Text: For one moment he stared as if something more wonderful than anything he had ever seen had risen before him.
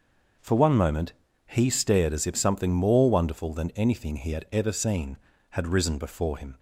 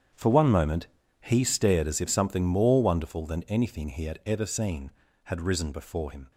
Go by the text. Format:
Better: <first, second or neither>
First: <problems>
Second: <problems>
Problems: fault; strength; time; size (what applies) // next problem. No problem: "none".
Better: first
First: starts louder than the rest; noticeable; until 1.7 s; 6 dB // pauses between "moment" and "he"; slight; at 1.1 s; 0.34 s long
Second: gets quieter; strong; throughout; 14 dB // starts louder than the rest; strong; until 1.4 s; 8.5 dB // pauses between "moment" and "he"; slight; at 0.8 s; 0.34 s long